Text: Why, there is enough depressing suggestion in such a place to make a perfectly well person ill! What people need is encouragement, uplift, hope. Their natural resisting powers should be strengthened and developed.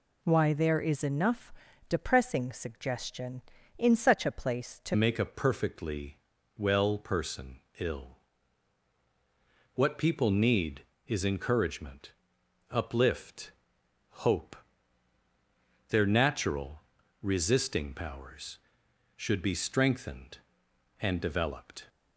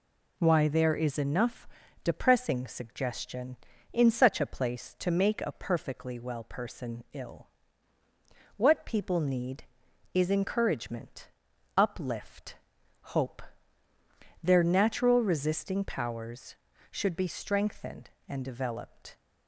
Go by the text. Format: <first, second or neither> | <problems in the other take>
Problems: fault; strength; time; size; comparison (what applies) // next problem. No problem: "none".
second | pauses between "enough" and "depressing"; at 1.5 s; 0.38 s long; also in the second // changes voice at "make"; from 4.9 s on; 16.9 s long // pauses between "perfectly" and "well"; at 6.1 s; 0.40 s long // pauses between "person" and "ill"; slight; at 7.6 s; 0.18 s long // pauses between "natural" and "resisting"; at 16.8 s; 0.40 s long